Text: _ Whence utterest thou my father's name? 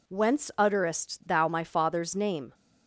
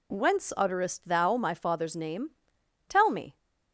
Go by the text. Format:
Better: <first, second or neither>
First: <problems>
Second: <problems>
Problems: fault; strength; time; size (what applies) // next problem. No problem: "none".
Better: first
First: none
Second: goes on to say "Tell me"; slight; from 2.8 s on; 0.48 s long